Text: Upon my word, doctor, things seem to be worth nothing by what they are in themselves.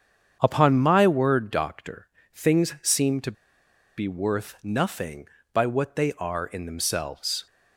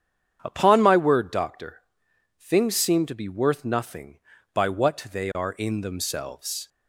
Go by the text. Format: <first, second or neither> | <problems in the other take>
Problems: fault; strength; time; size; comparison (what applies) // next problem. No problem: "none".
second | starts louder than the rest; strong; until 1.4 s; 8 dB; strong in the second // pauses between "to" and "be"; noticeable; at 3.3 s; 0.64 s long